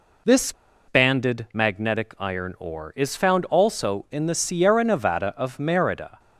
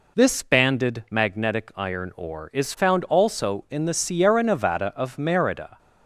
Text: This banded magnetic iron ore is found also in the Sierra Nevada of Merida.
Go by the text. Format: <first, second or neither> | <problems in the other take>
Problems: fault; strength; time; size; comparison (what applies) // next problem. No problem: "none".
second | pauses between "This" and "banded"; at 0.5 s; 0.36 s long